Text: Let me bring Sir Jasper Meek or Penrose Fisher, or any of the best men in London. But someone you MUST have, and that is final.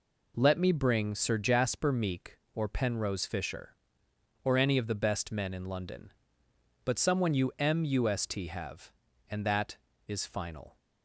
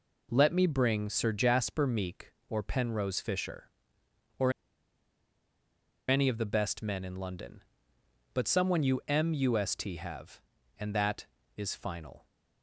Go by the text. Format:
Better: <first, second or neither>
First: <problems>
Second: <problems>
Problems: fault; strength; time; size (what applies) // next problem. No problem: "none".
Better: first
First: none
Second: pauses between "or" and "any"; strong; at 4.5 s; 1.5 s long